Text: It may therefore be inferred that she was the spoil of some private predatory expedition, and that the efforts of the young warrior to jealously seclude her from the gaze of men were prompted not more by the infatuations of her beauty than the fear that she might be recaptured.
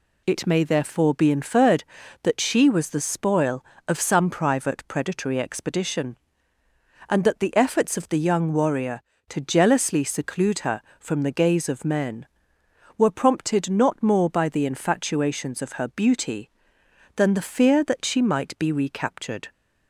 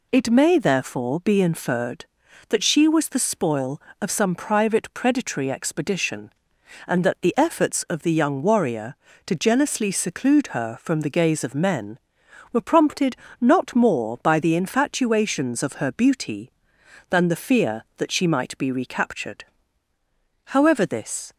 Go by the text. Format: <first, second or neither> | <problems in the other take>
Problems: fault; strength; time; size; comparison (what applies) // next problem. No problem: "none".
first | pauses between "prompted" and "not"; slight; at 13.1 s; 0.24 s long // goes on to say "However this"; noticeable; from 20.4 s on; 0.88 s long